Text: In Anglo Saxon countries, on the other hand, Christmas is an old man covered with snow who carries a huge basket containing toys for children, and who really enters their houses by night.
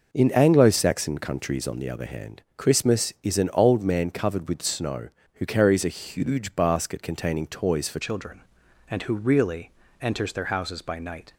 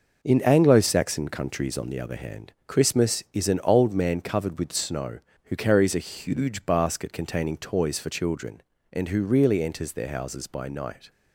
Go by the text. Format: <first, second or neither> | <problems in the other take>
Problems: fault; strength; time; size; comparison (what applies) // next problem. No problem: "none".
second | changes voice at "children"; from 8.0 s on; 3.3 s long // pauses between "really" and "enters"; slight; at 9.6 s; 0.30 s long